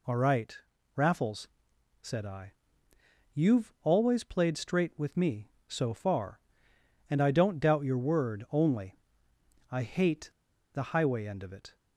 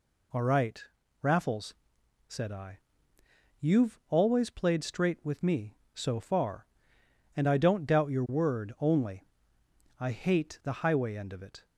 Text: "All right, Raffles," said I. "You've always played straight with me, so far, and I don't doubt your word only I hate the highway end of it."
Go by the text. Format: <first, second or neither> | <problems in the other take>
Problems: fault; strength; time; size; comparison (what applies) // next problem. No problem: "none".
second | pauses between "only" and "I"; noticeable; at 8.9 s; 0.72 s long; noticeable in the second // pauses between "hate" and "the"; at 10.2 s; 0.42 s long